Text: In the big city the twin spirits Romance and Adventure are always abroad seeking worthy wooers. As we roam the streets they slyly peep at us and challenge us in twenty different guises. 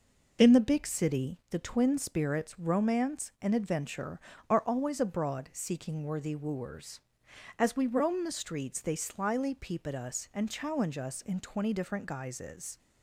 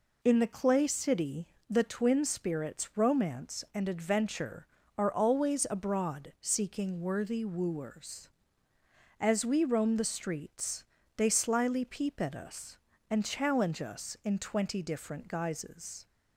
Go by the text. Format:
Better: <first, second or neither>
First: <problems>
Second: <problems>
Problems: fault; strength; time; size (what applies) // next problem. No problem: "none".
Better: first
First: none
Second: says "clay" for "big"; at 0.4 s // pauses between "city" and "the"; slight; at 1.4 s; 0.20 s long // pauses between "streets" and "they"; slight; at 10.8 s; 0.32 s long